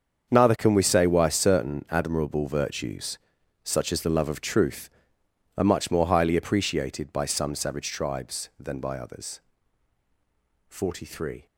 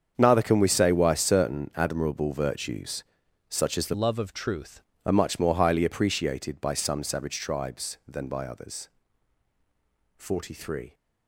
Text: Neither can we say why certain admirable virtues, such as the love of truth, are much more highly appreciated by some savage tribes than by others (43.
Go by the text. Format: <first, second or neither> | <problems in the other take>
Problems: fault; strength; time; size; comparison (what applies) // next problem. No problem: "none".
first | starts louder than the rest; strong; until 1.1 s; 7.5 dB; strong in the first // changes voice from "love" to "truth"; from 3.9 to 4.8 s; 0.9 s long